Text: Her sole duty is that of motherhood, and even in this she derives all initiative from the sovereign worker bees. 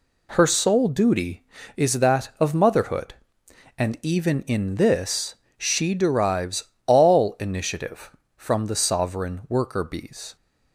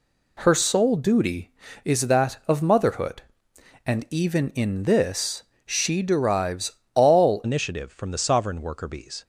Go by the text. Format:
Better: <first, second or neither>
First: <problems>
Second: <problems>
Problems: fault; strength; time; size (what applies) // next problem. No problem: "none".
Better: first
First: pauses between "this" and "she"; slight; at 5.3 s; 0.24 s long // pauses between "derives" and "all"; slight; at 6.6 s; 0.18 s long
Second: pauses between "this" and "she"; slight; at 5.4 s; 0.24 s long // pauses between "derives" and "all"; slight; at 6.7 s; 0.18 s long // changes voice at "initiative"; from 7.4 s on; 1.8 s long